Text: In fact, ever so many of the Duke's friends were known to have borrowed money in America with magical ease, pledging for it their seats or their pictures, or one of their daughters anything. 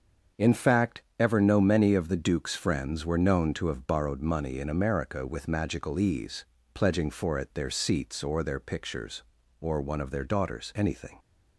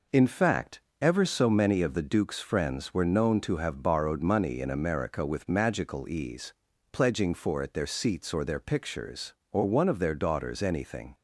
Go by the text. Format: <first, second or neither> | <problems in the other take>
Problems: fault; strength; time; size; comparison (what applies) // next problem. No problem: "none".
second | starts louder than the rest; until 1.5 s; 7 dB // says "no" for "so"; at 1.3 s